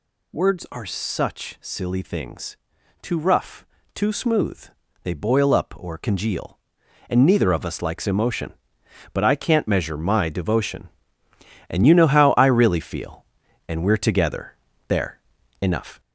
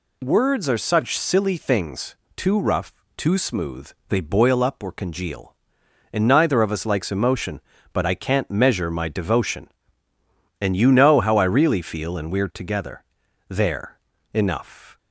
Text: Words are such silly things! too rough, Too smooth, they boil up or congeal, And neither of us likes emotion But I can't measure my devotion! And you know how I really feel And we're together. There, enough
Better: second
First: gets louder; noticeable; throughout; 4.5 dB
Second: none

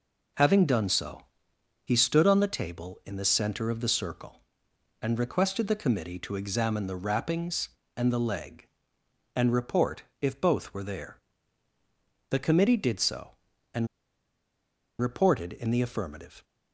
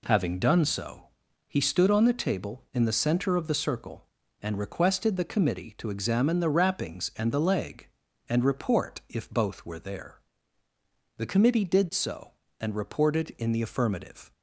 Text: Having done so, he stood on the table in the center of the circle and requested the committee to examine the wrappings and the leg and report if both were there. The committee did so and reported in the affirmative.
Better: second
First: pauses between "report" and "if"; slight; at 10.0 s; 0.18 s long // pauses between "and" and "reported"; at 13.8 s; 1.1 s long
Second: none

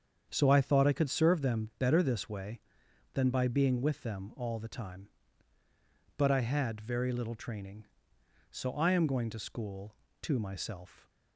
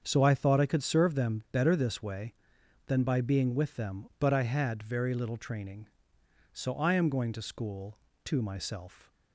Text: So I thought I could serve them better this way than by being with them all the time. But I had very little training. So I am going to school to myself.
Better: first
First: starts louder than the rest; strong; until 1.3 s; 7.5 dB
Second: starts louder than the rest; until 1.0 s; 7 dB // skips "all the time"; at 4.1 s

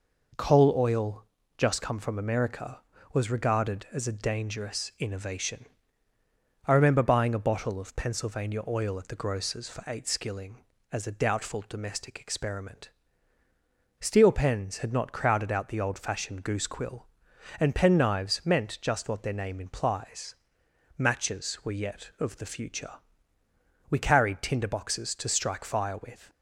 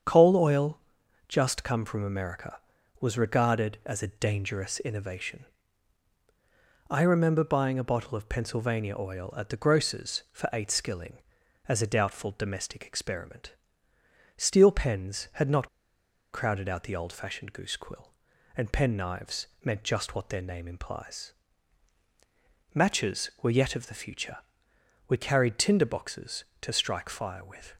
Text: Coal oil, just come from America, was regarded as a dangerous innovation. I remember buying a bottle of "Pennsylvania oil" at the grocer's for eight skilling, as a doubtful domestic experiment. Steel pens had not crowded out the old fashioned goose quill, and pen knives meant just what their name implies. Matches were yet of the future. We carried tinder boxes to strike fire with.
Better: first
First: none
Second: starts louder than the rest; strong; until 1.5 s; 8 dB // pauses between "not" and "crowded"; noticeable; at 15.6 s; 0.64 s long // pauses between "knives" and "meant"; slight; at 19.4 s; 0.16 s long

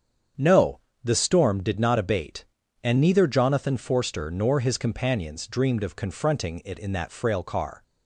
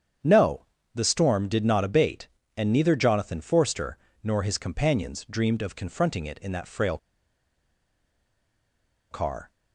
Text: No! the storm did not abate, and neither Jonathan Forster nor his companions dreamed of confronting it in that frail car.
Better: first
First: starts louder than the rest; strong; until 1.5 s; 7.5 dB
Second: starts louder than the rest; strong; until 1.5 s; 8 dB // pauses between "Forster" and "nor"; slight; at 3.9 s; 0.24 s long // pauses between "frail" and "car"; strong; at 6.9 s; 2.1 s long

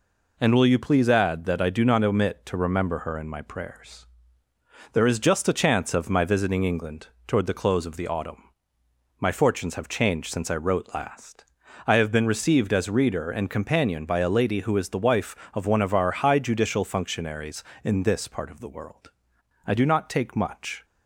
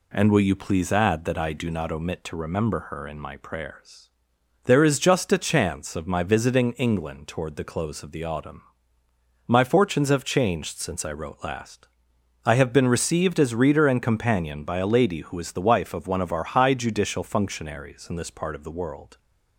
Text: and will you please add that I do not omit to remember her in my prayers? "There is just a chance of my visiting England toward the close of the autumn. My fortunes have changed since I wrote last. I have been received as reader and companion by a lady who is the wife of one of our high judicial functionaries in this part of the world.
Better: second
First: pauses between "England" and "toward"; slight; at 7.0 s; 0.18 s long // goes on to say "I do not take much"; noticeable; from 19.6 s on; 1.1 s long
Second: none

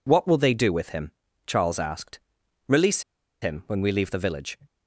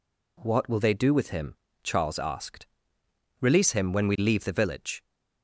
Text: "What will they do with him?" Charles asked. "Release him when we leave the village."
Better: second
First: pauses between "Release" and "him"; at 3.0 s; 0.40 s long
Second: none

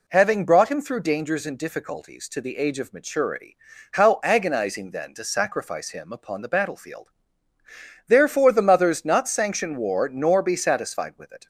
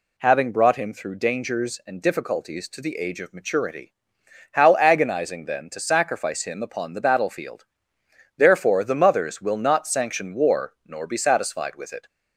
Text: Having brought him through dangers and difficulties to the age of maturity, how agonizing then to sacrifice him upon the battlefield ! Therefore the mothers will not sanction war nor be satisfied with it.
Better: second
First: skips "will"; at 9.0 s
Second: none

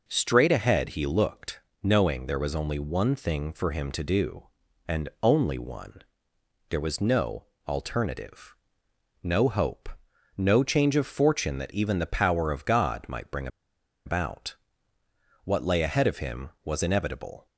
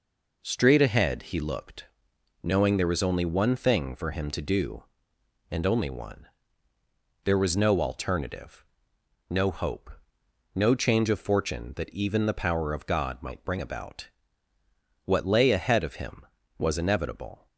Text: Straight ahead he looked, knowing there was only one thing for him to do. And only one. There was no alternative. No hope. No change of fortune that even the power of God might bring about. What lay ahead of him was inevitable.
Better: second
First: pauses between "no" and "alternative"; slight; at 7.4 s; 0.22 s long // pauses between "bring" and "about"; noticeable; at 13.4 s; 0.58 s long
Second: none

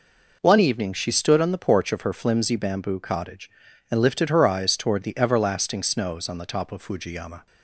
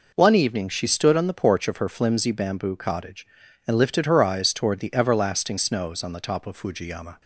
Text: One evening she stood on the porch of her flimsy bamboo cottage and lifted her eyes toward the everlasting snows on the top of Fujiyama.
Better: neither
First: none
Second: none

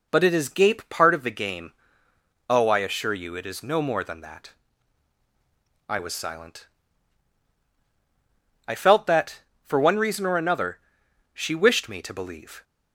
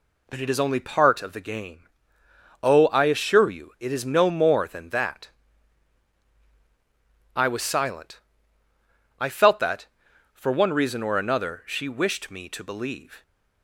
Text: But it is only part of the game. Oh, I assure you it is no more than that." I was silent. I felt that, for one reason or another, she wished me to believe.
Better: second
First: says "gape" for "only"; at 0.4 s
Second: none

